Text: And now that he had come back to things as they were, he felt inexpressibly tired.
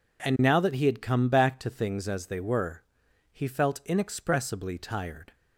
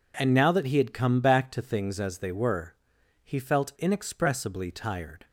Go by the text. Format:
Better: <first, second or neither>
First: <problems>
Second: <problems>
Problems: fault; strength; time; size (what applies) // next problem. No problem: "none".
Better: neither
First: none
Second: none